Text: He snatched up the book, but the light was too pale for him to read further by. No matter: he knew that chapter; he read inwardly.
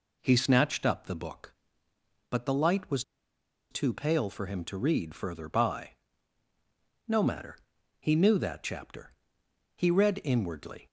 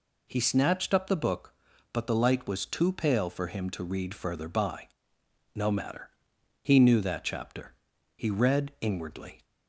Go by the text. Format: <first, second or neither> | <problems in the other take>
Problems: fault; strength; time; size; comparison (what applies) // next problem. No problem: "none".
second | pauses between "was" and "too"; noticeable; at 3.0 s; 0.68 s long